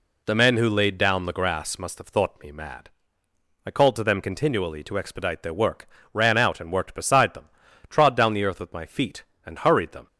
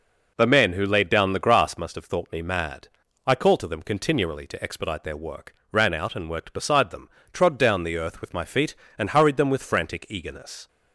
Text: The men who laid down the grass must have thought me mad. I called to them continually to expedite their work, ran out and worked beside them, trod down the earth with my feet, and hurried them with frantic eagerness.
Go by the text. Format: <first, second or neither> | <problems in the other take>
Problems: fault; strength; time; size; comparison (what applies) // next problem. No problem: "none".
second | stops before "with frantic eagerness"; at 10.0 s